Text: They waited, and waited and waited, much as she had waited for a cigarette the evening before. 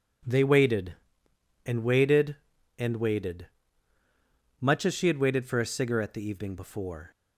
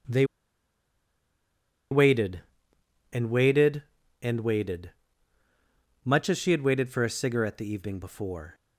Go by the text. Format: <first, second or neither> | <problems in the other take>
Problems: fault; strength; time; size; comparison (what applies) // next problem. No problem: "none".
first | pauses between "They" and "waited"; strong; at 0.2 s; 1.6 s long